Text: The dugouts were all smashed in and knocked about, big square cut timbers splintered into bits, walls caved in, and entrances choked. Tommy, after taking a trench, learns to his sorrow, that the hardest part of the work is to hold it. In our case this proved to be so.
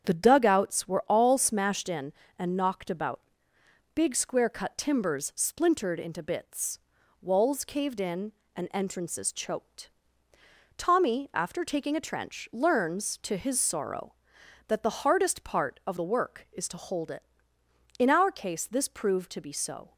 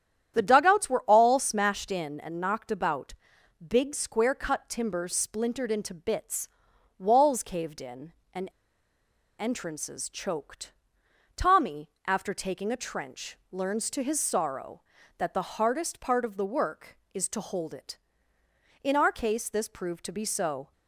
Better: first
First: starts louder than the rest; strong; until 1.1 s; 8 dB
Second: starts louder than the rest; strong; until 1.3 s; 10 dB // pauses between "and" and "entrances"; noticeable; at 8.4 s; 0.90 s long

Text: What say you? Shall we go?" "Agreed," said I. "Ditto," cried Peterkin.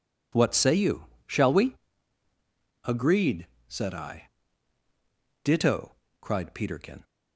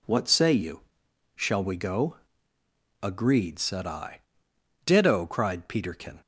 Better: second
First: skips "go"; at 2.3 s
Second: none

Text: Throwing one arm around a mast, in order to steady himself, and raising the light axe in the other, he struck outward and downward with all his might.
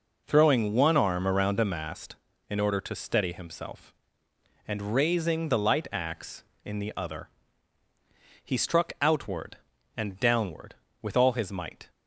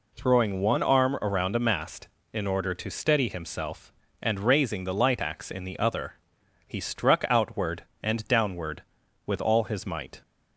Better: neither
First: none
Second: none

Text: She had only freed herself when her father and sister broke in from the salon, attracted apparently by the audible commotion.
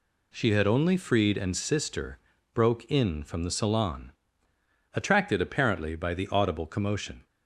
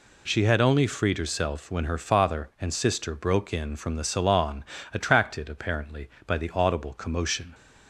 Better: second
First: skips "herself when her father"; at 1.3 s // pauses between "sister" and "broke"; slight; at 2.1 s; 0.36 s long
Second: none

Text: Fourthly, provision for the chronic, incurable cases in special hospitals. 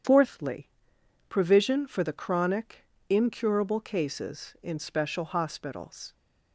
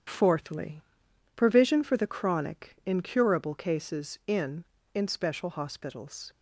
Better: first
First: starts louder than the rest; strong; until 1.6 s; 8.5 dB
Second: starts louder than the rest; strong; until 1.6 s; 9 dB // says "in" twice; at 4.9 s

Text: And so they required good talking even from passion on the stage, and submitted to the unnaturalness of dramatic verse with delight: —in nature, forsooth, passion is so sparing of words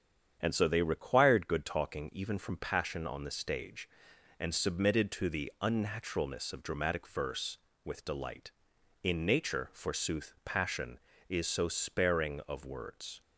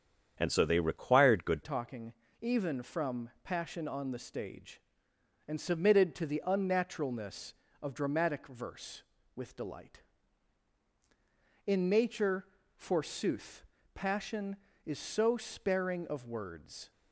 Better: first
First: starts louder than the rest; strong; until 1.4 s; 8 dB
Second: starts louder than the rest; strong; until 1.4 s; 8 dB // changes voice at "talking"; from 1.6 s on; 15.3 s long // pauses between "talking" and "even"; slight; at 2.1 s; 0.28 s long

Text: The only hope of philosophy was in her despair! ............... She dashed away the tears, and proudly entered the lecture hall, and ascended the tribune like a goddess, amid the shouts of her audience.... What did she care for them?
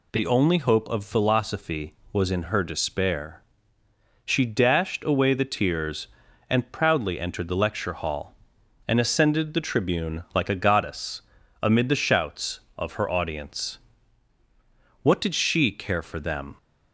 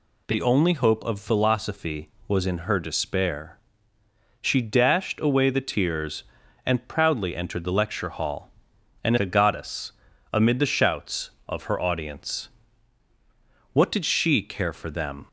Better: first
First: none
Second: skips "ascended the tribune like"; at 9.1 s

